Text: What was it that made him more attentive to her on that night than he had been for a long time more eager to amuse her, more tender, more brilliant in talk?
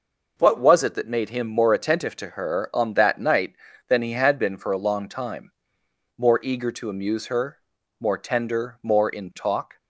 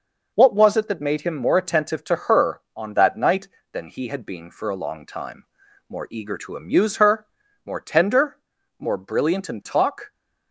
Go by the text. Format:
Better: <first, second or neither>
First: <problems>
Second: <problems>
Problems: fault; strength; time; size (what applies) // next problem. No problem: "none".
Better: second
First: pauses between "time" and "more"; noticeable; at 5.5 s; 0.68 s long // skips "brilliant"; at 9.0 s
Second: pauses between "time" and "more"; at 5.4 s; 0.44 s long